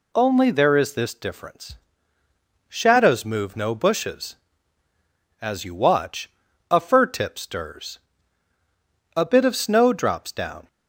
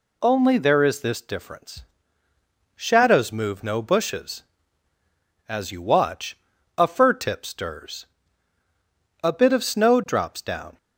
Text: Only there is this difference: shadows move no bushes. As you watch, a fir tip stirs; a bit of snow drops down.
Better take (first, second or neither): neither